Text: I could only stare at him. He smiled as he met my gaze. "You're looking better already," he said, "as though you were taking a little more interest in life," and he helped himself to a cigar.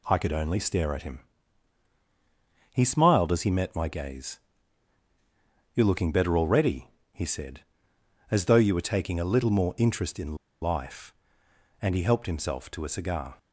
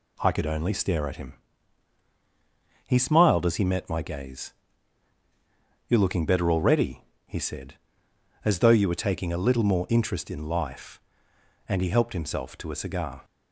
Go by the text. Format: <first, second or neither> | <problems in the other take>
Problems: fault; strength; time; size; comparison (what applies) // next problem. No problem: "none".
second | pauses between "in" and "life"; slight; at 10.3 s; 0.24 s long